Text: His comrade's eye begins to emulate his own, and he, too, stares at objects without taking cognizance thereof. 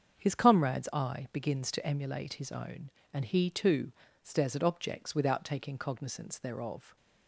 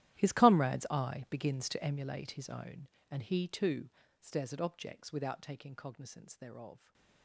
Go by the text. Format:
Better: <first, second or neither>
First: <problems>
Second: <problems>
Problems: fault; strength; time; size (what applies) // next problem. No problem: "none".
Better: first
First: starts louder than the rest; until 1.2 s; 7 dB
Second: gets quieter; strong; throughout; 19.5 dB // starts louder than the rest; strong; until 1.2 s; 13.5 dB